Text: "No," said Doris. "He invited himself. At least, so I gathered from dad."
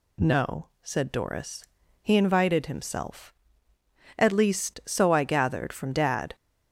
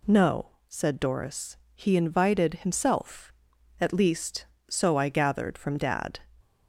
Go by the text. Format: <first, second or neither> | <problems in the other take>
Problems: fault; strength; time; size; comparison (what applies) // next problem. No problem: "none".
neither | none